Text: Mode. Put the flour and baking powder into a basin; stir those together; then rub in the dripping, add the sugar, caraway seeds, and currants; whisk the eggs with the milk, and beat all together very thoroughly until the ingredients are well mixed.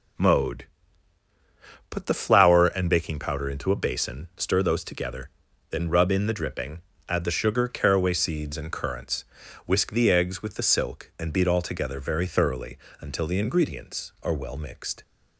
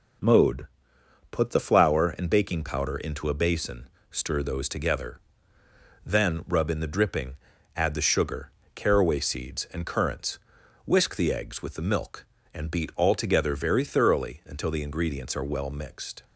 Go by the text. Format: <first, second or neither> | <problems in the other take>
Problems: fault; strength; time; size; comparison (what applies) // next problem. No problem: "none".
second | says "silk" for "milk"; at 10.6 s // pauses between "thoroughly" and "until"; slight; at 12.7 s; 0.22 s long